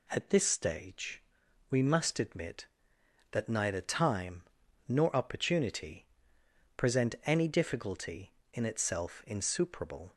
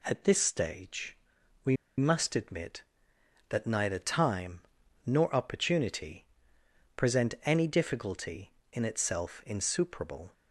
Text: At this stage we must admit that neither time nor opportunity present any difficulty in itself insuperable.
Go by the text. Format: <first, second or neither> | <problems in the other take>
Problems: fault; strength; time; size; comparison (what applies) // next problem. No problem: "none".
first | pauses between "stage" and "we"; noticeable; at 1.1 s; 0.48 s long; noticeable in the first // pauses between "we" and "must"; slight; at 1.7 s; 0.23 s long // pauses between "time" and "nor"; at 4.6 s; 0.44 s long; also in the first // pauses between "opportunity" and "present"; noticeable; at 6.2 s; 0.70 s long; noticeable in the first